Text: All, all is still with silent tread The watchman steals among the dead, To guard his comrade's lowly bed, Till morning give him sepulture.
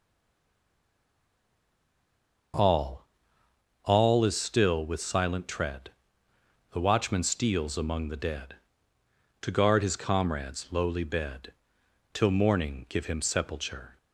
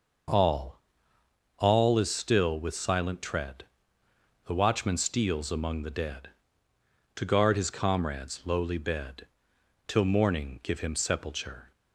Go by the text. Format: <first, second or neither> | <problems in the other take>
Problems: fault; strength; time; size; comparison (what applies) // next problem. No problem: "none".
second | stays silent before the first word; until 2.5 s; 2.5 s long // pauses between "tread" and "The"; noticeable; at 5.8 s; 0.82 s long; noticeable in the second